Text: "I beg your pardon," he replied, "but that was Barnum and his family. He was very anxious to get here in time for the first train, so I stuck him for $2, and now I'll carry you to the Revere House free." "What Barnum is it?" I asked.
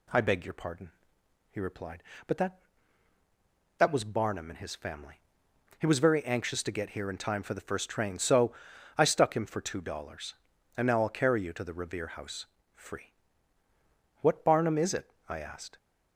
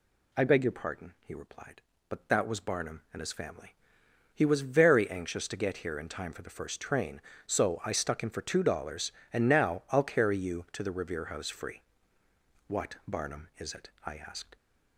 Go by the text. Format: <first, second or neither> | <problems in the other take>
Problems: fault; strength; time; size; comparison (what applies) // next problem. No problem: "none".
second | says "that" twice; at 3.7 s // pauses between "so" and "I"; at 8.5 s; 0.44 s long // pauses between "House" and "free"; slight; at 12.4 s; 0.28 s long